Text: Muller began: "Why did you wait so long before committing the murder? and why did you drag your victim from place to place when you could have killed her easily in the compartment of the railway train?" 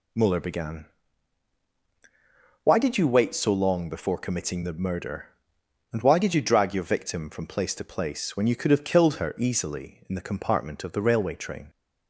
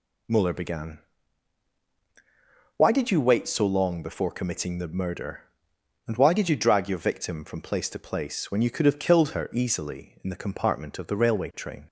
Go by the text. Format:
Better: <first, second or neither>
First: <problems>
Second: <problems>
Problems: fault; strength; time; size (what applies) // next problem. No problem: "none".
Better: neither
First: none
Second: none